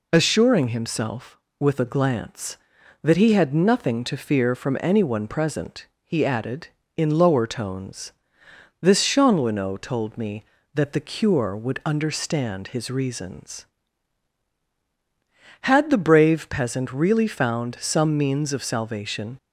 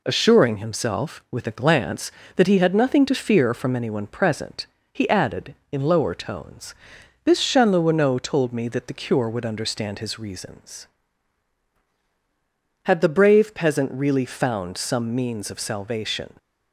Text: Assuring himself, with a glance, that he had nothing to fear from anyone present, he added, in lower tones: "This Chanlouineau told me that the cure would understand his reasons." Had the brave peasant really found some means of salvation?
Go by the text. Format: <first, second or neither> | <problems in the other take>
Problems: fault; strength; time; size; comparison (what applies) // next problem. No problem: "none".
neither | none